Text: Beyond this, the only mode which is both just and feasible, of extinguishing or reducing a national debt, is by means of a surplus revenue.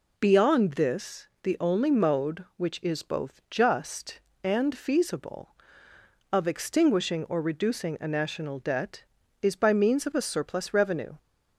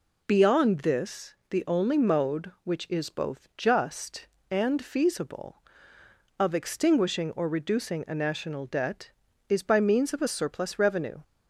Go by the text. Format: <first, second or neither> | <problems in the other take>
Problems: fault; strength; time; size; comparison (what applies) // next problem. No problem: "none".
neither | none